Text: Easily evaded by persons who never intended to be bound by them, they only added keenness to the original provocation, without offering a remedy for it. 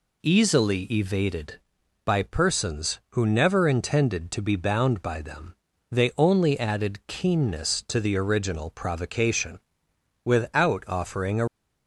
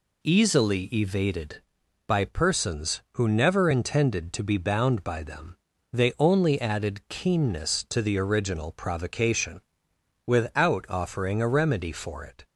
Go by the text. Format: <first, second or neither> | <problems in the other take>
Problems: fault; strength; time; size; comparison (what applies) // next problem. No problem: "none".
second | stops before "remedy for it"; at 11.4 s